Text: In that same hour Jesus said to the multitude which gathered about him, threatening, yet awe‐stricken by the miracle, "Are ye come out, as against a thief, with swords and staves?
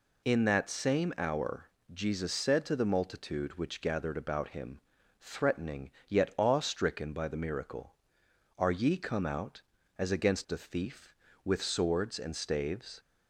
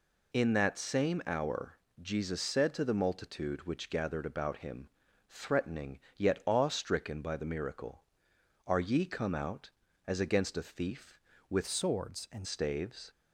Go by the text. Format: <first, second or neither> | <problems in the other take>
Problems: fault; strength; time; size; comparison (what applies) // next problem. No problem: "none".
first | pauses between "hour" and "Jesus"; slight; at 1.7 s; 0.24 s long; slight in the first // changes voice from "swords" to "and"; from 11.6 to 12.4 s; 0.8 s long